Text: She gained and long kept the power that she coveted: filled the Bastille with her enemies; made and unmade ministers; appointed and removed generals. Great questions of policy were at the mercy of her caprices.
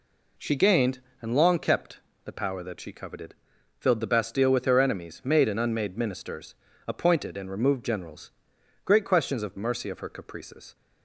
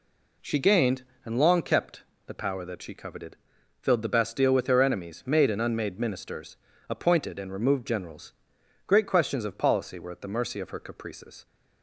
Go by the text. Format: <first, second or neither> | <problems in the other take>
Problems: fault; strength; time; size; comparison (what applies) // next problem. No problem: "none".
second | pauses between "kept" and "the"; slight; at 1.9 s; 0.24 s long; slight in the second // skips "policy were at the"; at 9.5 s